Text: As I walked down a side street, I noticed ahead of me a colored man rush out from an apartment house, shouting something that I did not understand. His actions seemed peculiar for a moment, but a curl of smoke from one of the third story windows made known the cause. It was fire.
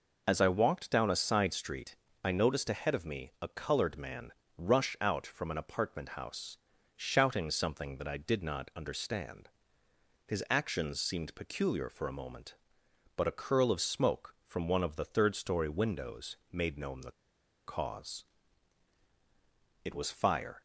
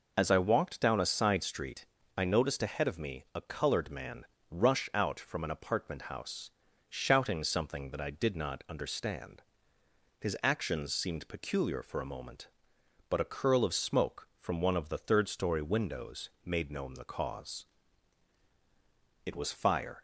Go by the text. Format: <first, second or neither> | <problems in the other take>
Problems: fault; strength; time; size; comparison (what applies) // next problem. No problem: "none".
second | pauses between "man" and "rush"; slight; at 4.3 s; 0.24 s long; slight in the second // pauses between "the" and "cause"; noticeable; at 17.1 s; 0.54 s long